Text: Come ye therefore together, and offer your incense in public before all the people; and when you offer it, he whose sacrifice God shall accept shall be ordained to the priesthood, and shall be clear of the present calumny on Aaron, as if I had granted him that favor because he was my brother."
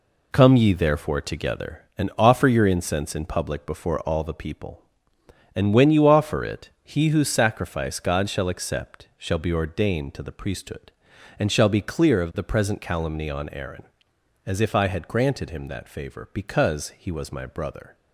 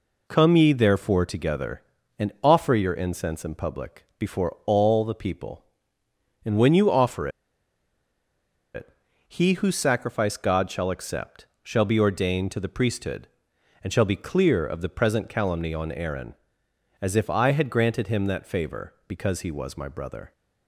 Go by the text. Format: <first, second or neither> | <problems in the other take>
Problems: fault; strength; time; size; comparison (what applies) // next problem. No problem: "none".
first | pauses between "offer" and "it"; strong; at 7.2 s; 1.4 s long // pauses between "accept" and "shall"; slight; at 11.4 s; 0.16 s long